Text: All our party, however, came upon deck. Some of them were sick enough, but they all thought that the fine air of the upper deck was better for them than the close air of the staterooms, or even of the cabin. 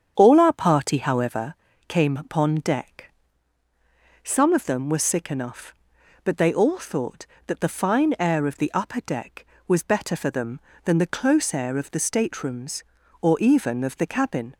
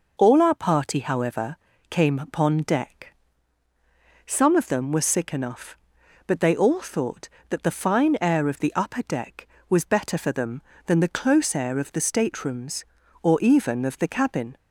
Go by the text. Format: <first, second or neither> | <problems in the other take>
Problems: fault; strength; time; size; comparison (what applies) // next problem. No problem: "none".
second | starts louder than the rest; strong; until 1.4 s; 8 dB